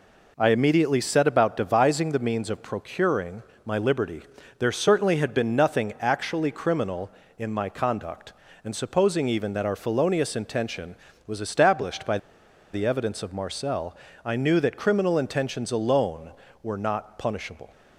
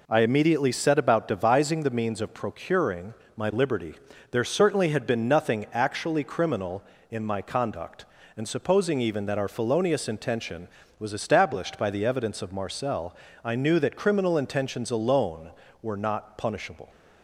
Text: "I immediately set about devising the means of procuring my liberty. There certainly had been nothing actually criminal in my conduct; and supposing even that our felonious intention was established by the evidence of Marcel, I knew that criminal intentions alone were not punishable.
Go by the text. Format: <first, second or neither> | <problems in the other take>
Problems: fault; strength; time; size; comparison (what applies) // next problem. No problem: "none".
second | pauses between "procuring" and "my"; slight; at 3.4 s; 0.20 s long; slight in the second // pauses between "by" and "the"; noticeable; at 12.1 s; 0.55 s long